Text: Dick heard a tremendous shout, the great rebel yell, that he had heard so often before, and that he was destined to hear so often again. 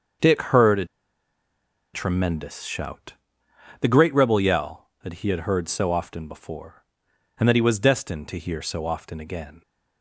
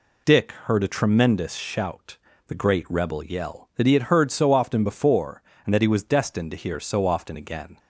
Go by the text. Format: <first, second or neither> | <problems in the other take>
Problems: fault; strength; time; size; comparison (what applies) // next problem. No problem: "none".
second | starts louder than the rest; until 2.3 s; 7 dB // pauses between "a" and "tremendous"; at 0.8 s; 1.0 s long